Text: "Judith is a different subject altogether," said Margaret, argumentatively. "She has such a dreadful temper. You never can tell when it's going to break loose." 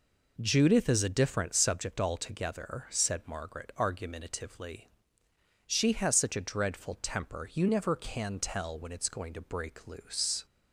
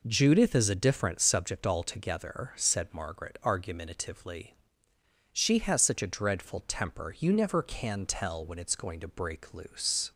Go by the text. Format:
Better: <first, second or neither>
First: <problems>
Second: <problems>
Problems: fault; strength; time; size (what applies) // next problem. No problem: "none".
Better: neither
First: none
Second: none